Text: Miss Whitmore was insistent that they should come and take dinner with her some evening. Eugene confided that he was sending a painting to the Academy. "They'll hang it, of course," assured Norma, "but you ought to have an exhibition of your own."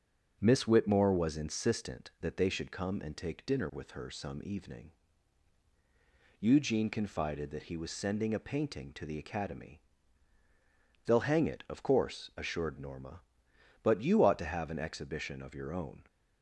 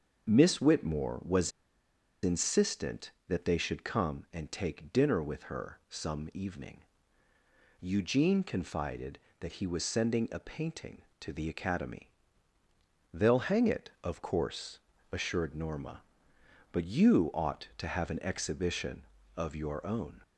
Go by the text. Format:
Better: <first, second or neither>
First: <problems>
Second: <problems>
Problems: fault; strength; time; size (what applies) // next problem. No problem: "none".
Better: first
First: starts louder than the rest; until 1.4 s; 6.5 dB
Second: starts louder than the rest; until 1.3 s; 6.5 dB // pauses between "was" and "insistent"; noticeable; at 1.5 s; 0.75 s long